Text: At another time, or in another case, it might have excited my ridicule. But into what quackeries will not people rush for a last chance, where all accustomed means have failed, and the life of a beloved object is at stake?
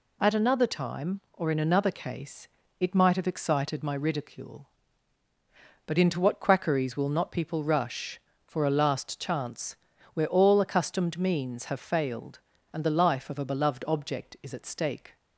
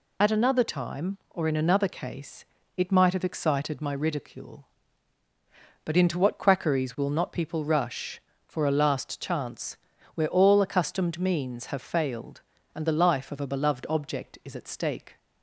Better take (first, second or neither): first